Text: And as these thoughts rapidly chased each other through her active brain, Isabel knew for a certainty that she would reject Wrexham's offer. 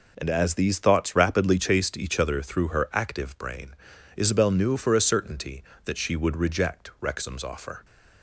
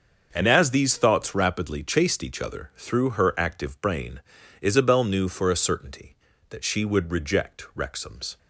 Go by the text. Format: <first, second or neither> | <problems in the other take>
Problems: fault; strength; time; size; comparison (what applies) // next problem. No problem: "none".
first | starts louder than the rest; until 1.3 s; 6.5 dB // stops before "offer"; at 8.3 s